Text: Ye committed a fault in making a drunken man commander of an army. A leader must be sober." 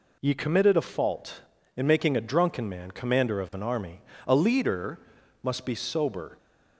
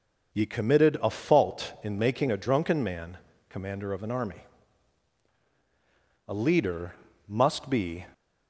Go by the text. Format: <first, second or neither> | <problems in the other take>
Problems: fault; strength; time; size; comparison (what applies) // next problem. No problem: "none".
first | pauses between "man" and "commander"; slight; at 3.1 s; 0.30 s long // pauses between "leader" and "must"; slight; at 6.9 s; 0.34 s long; also in the first // stops before "sober"; at 8.1 s